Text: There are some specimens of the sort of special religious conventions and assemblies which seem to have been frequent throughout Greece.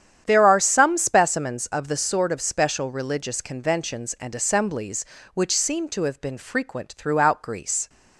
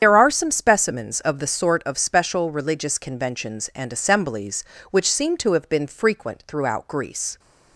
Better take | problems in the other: first | loses the start of "There"; at 0.0 s; 85 ms // starts louder than the rest; strong; until 1.0 s; 8.5 dB; strong in the first

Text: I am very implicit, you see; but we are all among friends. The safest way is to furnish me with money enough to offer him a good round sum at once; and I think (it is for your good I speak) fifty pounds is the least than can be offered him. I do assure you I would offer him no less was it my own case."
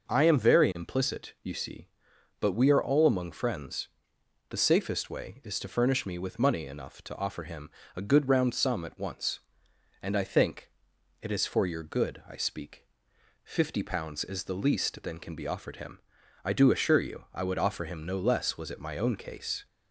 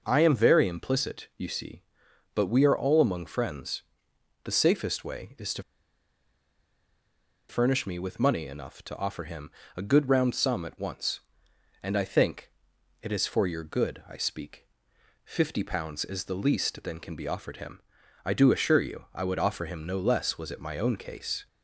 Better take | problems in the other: first | pauses between "to" and "furnish"; strong; at 5.6 s; 1.8 s long // pauses between "him" and "a"; slight; at 9.4 s; 0.26 s long; slight in the first

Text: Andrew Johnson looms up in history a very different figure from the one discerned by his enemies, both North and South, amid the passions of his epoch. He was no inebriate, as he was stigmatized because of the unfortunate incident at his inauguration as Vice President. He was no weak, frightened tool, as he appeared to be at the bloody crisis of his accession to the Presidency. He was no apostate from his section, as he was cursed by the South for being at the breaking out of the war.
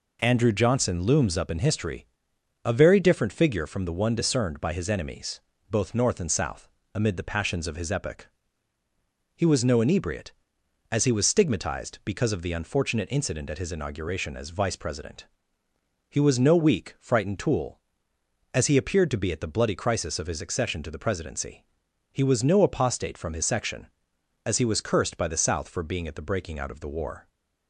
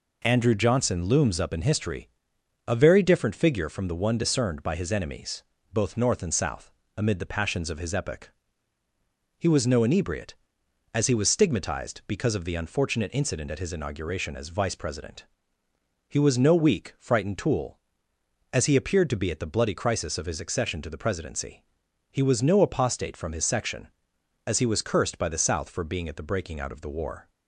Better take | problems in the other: neither | pauses between "history" and "a"; noticeable; the same in both

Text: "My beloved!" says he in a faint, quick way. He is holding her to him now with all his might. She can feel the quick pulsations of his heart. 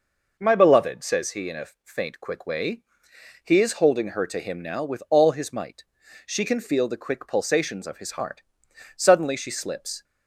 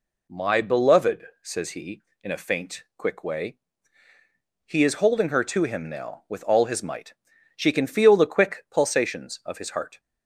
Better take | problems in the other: second | pauses between "a" and "faint"; slight; at 1.6 s; 0.18 s long // goes on to say "Suddenly she slips"; noticeable; from 8.9 s on; 1.0 s long

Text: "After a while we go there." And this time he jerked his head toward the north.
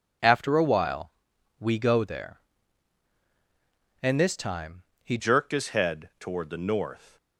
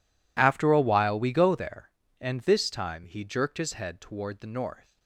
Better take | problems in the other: second | pauses between "while" and "we"; noticeable; at 1.1 s; 0.48 s long // pauses between "time" and "he"; slight; at 4.8 s; 0.22 s long // changes voice at "jerked"; from 5.1 s on; 2.0 s long

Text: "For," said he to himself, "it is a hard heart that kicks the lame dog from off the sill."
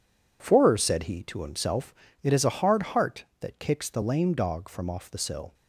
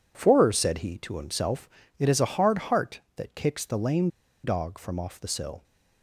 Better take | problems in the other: first | pauses between "lame" and "dog"; slight; at 4.0 s; 0.35 s long

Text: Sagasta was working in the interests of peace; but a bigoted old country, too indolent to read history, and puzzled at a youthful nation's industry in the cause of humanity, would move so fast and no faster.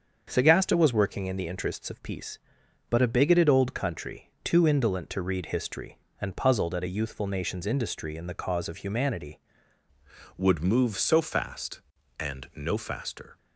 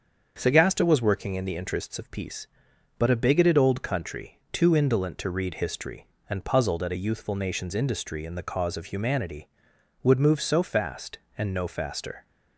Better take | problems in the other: second | starts louder than the rest; until 1.2 s; 7 dB; also in the second // changes voice at "would"; from 10.3 s on; 3.0 s long

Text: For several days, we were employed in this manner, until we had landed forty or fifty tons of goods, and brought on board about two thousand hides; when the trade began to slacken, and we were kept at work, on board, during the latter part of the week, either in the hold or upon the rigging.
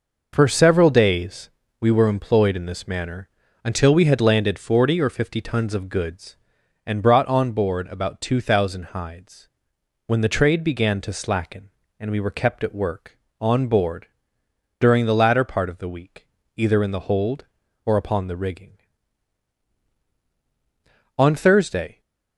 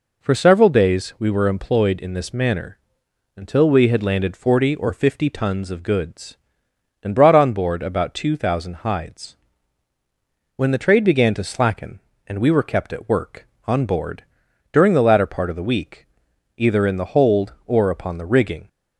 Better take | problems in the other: second | goes on to say "On Thursday"; noticeable; from 21.1 s on; 0.84 s long

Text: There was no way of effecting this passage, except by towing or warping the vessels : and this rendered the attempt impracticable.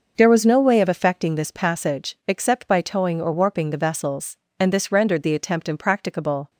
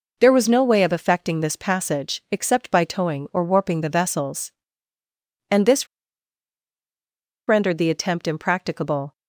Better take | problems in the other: first | pauses between "this" and "rendered"; strong; at 5.8 s; 1.6 s long

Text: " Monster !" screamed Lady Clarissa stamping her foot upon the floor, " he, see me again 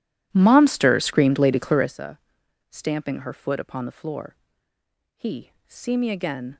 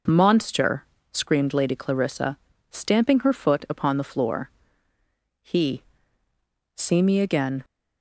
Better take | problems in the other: second | starts louder than the rest; strong; until 2.0 s; 13.5 dB // pauses between "Clarissa" and "stamping"; noticeable; at 2.1 s; 0.52 s long; slight in the second

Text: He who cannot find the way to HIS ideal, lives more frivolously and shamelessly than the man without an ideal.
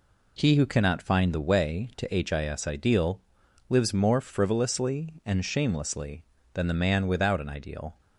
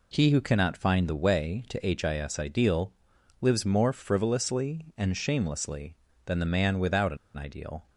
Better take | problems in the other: first | pauses between "an" and "ideal"; slight; at 7.1 s; 0.19 s long

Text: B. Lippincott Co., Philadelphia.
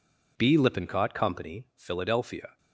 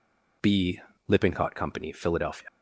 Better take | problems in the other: first | leaves "Philadelphia" unfinished; at 2.4 s; 60 ms

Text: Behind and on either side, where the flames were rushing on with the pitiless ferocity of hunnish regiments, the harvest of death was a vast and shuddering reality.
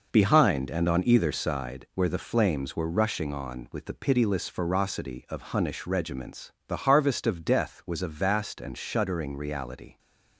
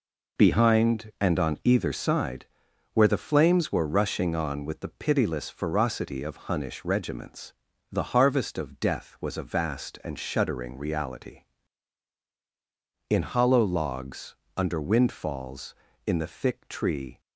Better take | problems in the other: first | goes on to say "In hollow logs under windfalls in the thick tree"; strong; from 13.0 s on; 4.1 s long

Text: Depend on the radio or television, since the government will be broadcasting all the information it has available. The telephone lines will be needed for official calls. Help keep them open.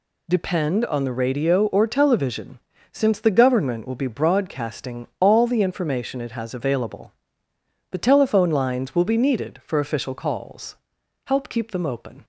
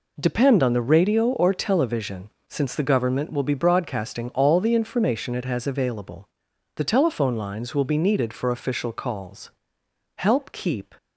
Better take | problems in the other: first | stops before "them open"; at 10.9 s

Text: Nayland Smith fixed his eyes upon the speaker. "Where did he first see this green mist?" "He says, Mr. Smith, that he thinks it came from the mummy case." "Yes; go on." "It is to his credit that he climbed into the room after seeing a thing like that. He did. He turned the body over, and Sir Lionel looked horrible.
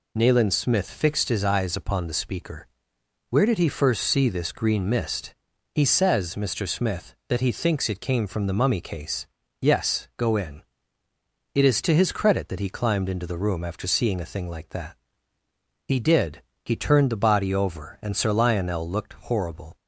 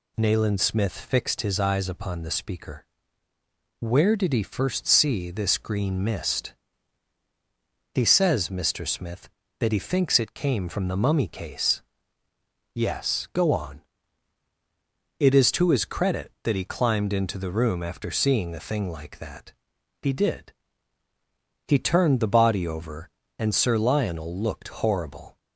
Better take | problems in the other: second | says "in" for "on"; at 10.3 s

